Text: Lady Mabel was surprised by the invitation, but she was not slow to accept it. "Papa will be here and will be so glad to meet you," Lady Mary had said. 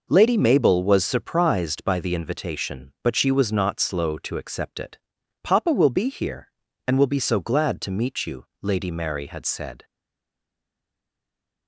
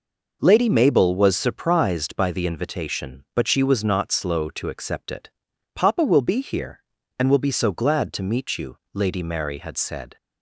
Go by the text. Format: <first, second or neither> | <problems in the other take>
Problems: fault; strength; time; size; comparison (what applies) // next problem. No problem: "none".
second | stays silent after the last word; noticeable; from 9.8 s on; 1.8 s long